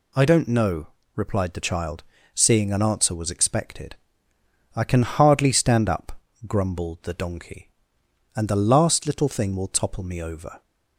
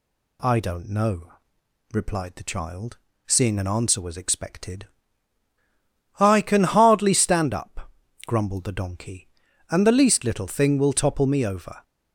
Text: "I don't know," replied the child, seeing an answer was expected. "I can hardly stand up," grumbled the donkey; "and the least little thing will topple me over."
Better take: second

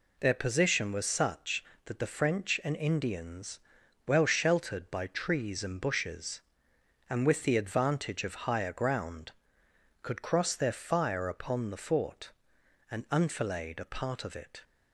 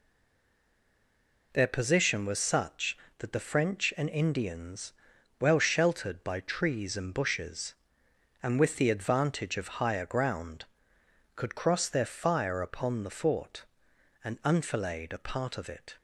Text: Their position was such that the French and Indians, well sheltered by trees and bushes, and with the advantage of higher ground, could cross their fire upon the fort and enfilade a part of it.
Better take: first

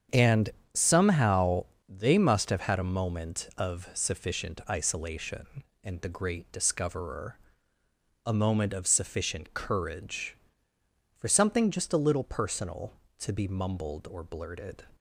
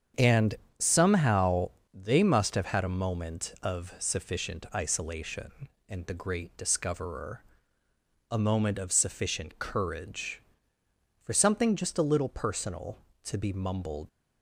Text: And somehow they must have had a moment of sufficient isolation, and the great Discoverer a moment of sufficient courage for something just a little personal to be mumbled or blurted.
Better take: first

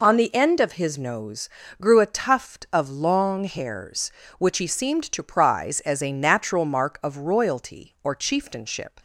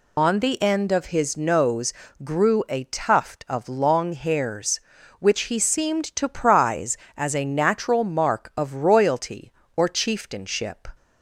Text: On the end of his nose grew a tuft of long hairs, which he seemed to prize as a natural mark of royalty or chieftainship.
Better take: first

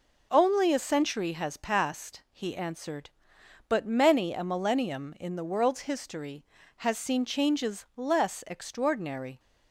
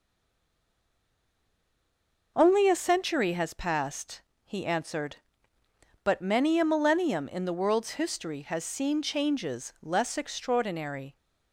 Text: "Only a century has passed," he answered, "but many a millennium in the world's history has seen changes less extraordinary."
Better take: first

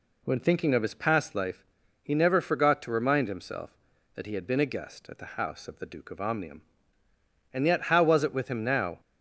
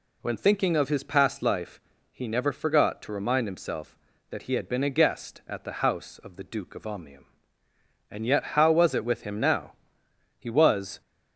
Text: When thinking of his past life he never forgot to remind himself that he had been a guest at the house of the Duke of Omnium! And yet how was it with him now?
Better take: first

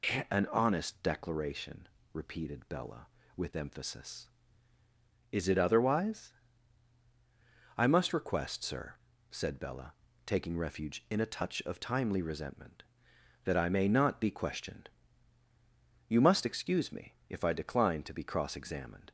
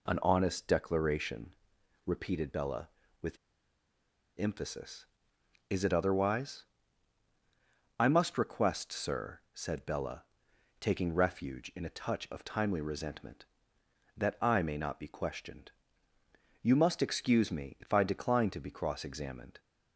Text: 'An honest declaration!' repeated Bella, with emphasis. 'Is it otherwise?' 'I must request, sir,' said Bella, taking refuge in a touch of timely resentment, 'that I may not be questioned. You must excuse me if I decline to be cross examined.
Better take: first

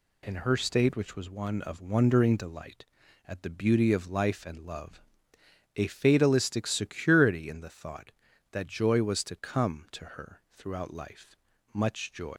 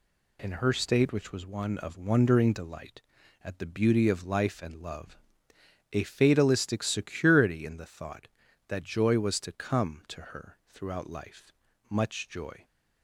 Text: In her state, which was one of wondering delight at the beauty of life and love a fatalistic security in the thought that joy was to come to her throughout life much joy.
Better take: second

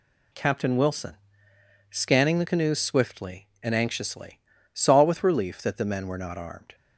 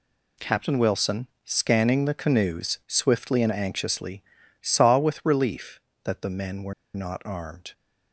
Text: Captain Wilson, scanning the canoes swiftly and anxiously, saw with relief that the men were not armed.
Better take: first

